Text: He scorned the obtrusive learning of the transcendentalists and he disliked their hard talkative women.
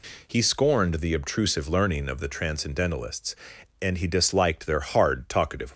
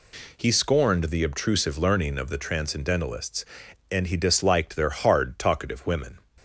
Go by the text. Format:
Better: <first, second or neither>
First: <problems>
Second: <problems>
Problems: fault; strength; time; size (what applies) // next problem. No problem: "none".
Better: second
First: stops before "women"; at 5.7 s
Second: none